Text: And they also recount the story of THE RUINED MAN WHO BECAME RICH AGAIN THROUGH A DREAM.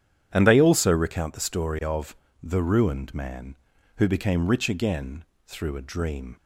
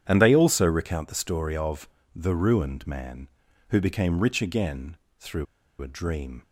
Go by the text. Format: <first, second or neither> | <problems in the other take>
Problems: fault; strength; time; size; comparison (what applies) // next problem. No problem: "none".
first | starts louder than the rest; strong; until 1.0 s; 9 dB; strong in the first // pauses between "of" and "THE"; slight; at 1.8 s; 0.26 s long; slight in the first // pauses between "AGAIN" and "THROUGH"; slight; at 4.9 s; 0.22 s long; slight in the first // pauses between "THROUGH" and "A"; at 5.4 s; 0.36 s long